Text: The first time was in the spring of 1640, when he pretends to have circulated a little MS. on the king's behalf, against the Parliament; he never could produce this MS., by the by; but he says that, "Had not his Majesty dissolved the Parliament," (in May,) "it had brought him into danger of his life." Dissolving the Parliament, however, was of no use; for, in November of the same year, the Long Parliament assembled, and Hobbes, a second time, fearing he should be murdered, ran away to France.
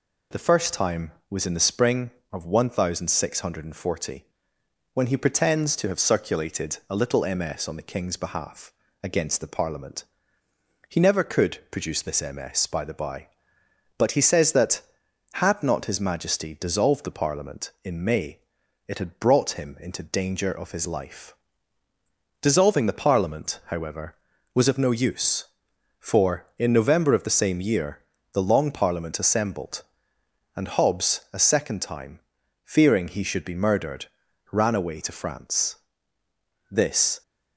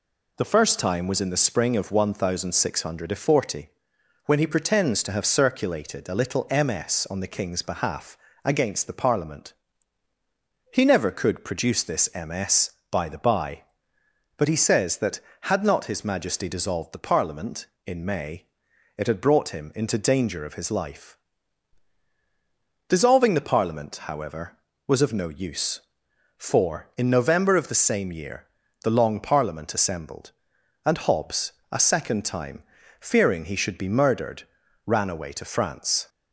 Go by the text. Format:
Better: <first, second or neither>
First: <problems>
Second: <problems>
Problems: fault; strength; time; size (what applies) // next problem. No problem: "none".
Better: second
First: goes on to say "This"; from 36.6 s on; 0.52 s long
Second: none